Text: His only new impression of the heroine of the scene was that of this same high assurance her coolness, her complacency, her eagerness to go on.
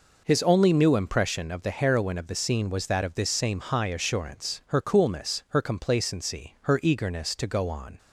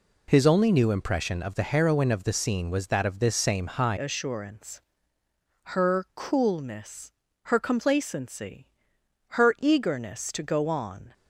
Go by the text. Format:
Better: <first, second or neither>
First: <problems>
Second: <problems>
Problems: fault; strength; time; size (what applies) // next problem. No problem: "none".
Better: first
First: none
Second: changes voice at "assurance"; from 3.9 s on; 7.2 s long // pauses between "assurance" and "her"; noticeable; at 4.8 s; 0.94 s long